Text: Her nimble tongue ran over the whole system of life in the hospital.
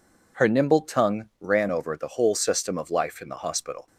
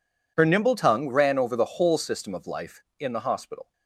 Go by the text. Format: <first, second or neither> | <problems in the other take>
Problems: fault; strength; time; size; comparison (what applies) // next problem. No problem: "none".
neither | none